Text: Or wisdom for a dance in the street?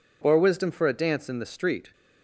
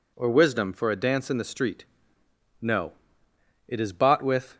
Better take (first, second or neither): first